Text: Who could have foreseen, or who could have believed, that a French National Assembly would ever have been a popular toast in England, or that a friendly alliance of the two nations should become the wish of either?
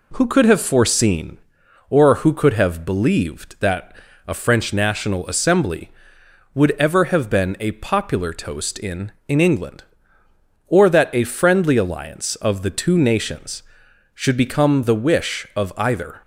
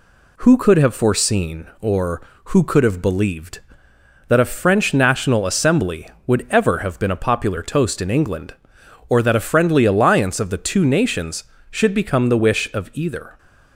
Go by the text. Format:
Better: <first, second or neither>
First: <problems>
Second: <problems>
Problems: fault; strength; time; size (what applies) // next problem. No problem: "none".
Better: second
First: pauses between "that" and "a"; slight; at 3.9 s; 0.30 s long // says "in" twice; at 9.2 s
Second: none